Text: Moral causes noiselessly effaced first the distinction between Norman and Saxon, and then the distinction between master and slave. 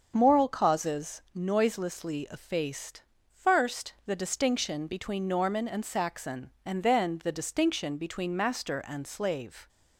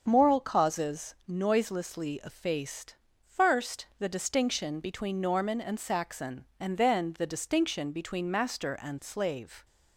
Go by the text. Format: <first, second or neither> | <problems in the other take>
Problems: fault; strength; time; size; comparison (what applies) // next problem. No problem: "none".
neither | starts louder than the rest; the same in both // pauses between "effaced" and "first"; slight; the same in both